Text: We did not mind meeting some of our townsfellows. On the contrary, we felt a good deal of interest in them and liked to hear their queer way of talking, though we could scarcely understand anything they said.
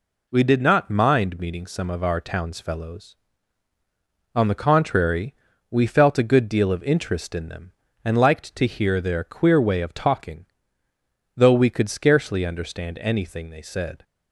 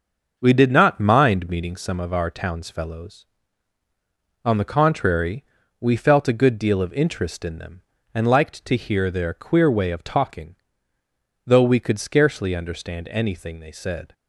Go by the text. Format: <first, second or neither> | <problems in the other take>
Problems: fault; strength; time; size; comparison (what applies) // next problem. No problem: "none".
first | starts louder than the rest; until 2.0 s; 6 dB